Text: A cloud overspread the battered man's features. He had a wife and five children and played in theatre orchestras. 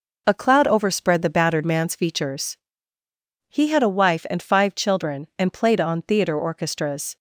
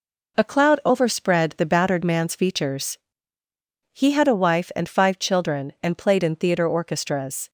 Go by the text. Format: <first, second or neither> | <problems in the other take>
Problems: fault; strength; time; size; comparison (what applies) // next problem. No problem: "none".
second | says "on" for "in"; at 5.8 s